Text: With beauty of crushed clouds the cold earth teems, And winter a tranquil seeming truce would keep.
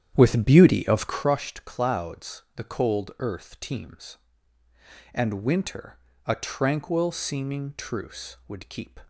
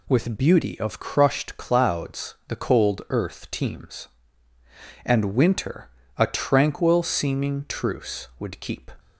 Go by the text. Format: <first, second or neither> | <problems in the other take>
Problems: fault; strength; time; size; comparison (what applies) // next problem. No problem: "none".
second | starts louder than the rest; strong; until 1.3 s; 10 dB // pauses between "winter" and "a"; slight; at 5.9 s; 0.30 s long; slight in the second